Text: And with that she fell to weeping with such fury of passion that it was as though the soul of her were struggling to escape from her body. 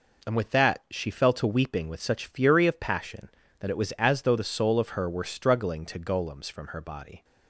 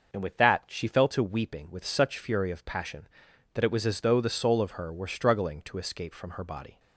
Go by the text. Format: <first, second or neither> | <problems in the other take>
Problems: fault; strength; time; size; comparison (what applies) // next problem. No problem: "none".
second | says "golems" for "escape"; at 5.9 s